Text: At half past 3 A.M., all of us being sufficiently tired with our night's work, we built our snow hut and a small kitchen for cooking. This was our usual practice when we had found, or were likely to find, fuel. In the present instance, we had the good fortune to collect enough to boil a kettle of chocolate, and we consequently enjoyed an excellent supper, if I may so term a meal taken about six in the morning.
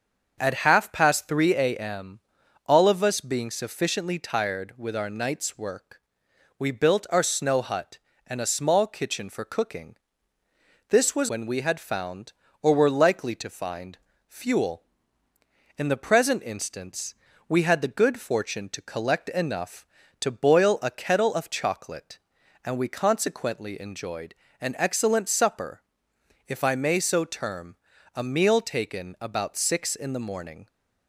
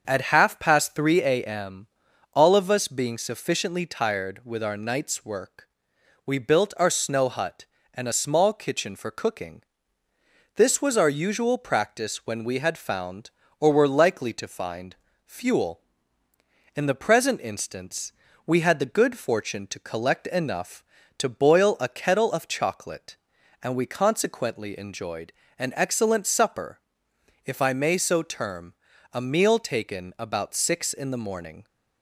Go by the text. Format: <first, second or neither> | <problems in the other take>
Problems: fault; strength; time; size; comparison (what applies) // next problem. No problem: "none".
second | starts louder than the rest; until 1.4 s; 6.5 dB; also in the second // skips "our usual practice"; at 11.2 s // pauses between "enjoyed" and "an"; slight; at 24.3 s; 0.24 s long; slight in the second // pauses between "term" and "a"; at 27.7 s; 0.38 s long; also in the second